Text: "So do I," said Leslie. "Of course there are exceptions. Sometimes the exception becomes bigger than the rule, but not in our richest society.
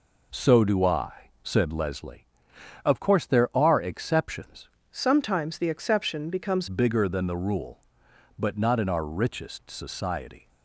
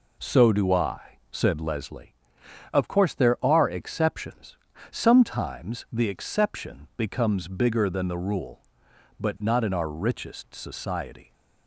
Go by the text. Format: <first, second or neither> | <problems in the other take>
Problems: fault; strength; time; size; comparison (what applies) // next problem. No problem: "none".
second | changes voice from "Sometimes" to "becomes"; from 4.9 to 6.6 s; 1.7 s long